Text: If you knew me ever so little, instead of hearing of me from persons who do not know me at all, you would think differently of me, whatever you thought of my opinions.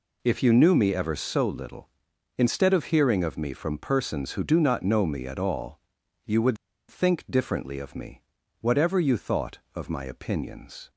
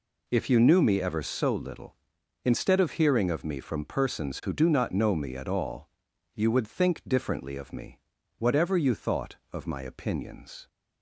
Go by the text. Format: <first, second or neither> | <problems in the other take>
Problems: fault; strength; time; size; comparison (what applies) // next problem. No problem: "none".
second | pauses between "would" and "think"; slight; at 6.5 s; 0.33 s long